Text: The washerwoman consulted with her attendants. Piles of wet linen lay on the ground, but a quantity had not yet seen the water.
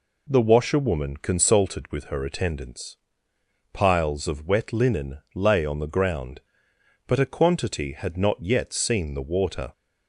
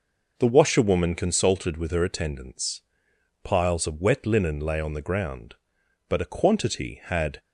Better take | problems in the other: first | stops before "not yet seen the water"; at 7.3 s

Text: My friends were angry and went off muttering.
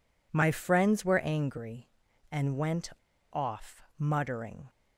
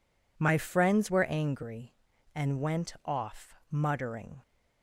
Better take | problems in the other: second | pauses between "went" and "off"; at 2.9 s; 0.41 s long // pauses between "off" and "muttering"; slight; at 3.8 s; 0.16 s long; slight in the second

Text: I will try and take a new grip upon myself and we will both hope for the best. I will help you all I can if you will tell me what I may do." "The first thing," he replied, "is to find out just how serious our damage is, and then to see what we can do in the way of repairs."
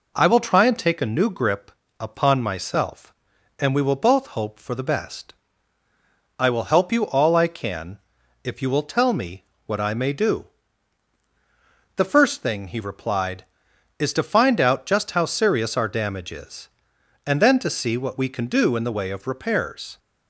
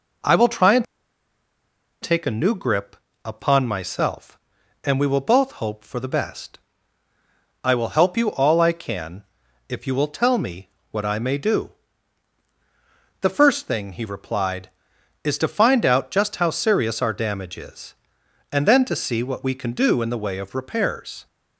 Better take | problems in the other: first | pauses between "and" and "take"; at 0.8 s; 1.1 s long // pauses between "grip" and "upon"; slight; at 2.9 s; 0.28 s long; slight in the first // pauses between "can" and "if"; at 9.2 s; 0.44 s long; also in the first // pauses between "me" and "what"; slight; at 10.6 s; 0.24 s long; slight in the first

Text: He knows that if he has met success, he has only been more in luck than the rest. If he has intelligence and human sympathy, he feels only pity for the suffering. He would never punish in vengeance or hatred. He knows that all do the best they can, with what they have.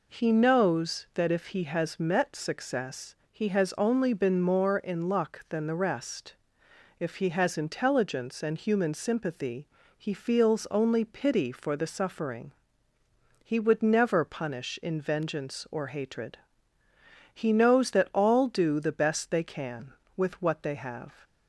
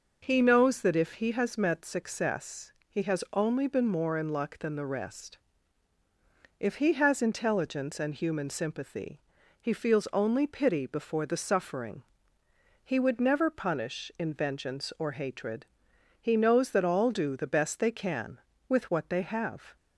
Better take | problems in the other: first | says "before" for "for"; at 10.8 s

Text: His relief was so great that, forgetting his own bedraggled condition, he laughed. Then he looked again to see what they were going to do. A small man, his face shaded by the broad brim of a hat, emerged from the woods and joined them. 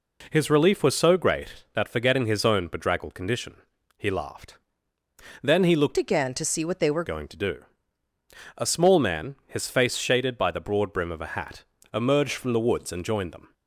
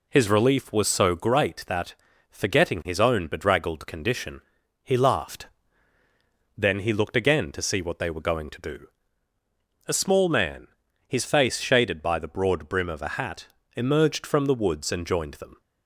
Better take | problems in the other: second | changes voice from "again" to "were"; from 5.9 to 7.0 s; 1.1 s long

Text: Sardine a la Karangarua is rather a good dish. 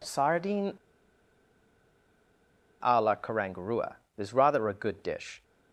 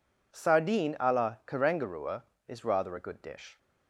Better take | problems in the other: second | pauses between "Sardine" and "a"; strong; at 0.7 s; 2.0 s long

